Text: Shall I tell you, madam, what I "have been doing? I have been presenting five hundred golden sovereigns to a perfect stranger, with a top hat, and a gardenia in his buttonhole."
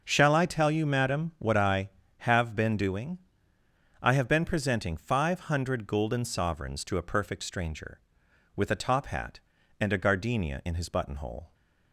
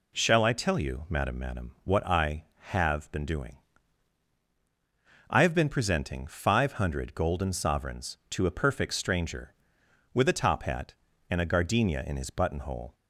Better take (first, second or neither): first